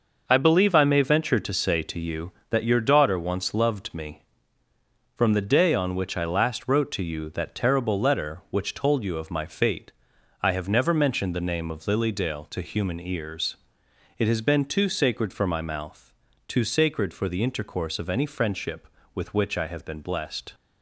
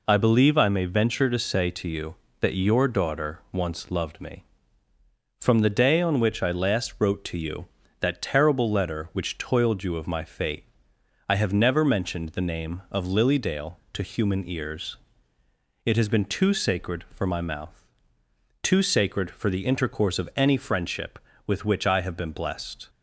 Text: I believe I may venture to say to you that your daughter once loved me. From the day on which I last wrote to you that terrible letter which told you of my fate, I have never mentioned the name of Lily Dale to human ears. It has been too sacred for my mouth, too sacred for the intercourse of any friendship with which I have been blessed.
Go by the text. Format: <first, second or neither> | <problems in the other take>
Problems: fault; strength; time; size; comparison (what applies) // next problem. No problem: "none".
first | says "toiled" for "told"; at 9.3 s